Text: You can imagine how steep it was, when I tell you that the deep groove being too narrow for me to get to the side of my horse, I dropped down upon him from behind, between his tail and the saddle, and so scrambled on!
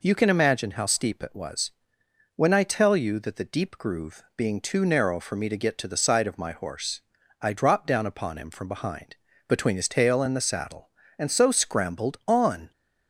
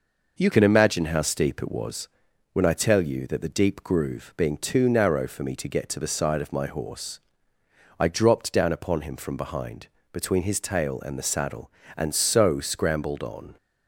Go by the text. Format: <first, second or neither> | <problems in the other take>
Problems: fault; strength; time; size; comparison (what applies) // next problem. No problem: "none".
first | changes voice at "can"; from 0.5 s on; 13.0 s long